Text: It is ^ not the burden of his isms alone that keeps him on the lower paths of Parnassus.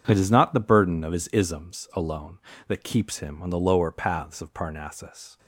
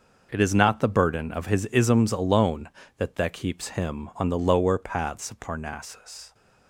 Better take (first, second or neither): first